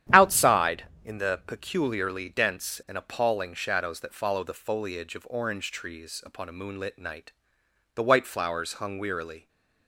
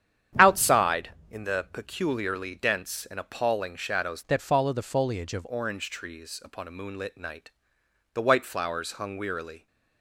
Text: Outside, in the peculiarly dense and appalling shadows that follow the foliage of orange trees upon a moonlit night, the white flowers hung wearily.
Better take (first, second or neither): first